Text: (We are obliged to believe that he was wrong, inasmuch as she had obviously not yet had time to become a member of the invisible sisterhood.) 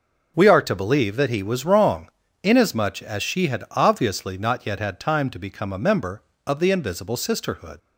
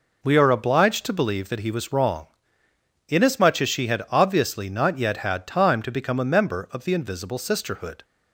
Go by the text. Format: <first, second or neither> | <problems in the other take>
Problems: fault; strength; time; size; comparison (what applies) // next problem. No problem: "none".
second | skips "obliged"; at 0.6 s